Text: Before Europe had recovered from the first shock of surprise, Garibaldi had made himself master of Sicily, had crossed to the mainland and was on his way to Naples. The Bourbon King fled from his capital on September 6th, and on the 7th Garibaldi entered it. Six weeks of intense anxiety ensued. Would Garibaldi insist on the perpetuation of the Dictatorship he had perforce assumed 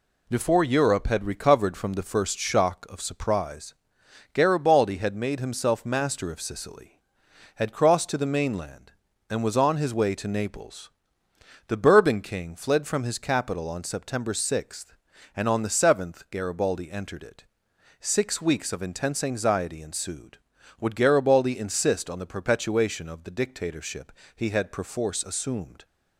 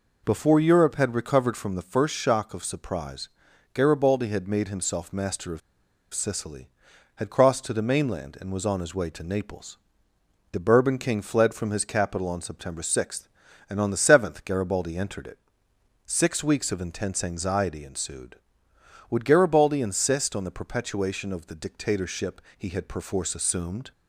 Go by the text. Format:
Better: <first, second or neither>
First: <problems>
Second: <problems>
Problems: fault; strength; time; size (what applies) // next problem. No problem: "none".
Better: first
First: pauses between "Dictatorship" and "he"; slight; at 24.1 s; 0.26 s long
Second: pauses between "of" and "Sicily"; noticeable; at 5.6 s; 0.53 s long // pauses between "Dictatorship" and "he"; slight; at 22.4 s; 0.16 s long